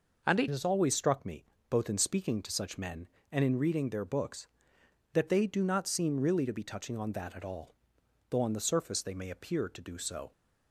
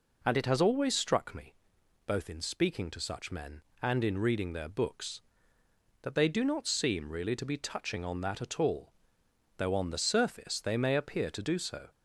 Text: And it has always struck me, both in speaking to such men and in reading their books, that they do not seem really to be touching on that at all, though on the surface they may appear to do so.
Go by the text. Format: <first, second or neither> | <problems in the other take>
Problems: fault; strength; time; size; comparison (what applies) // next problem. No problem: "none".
second | changes voice at "has"; from 0.4 s on; 9.9 s long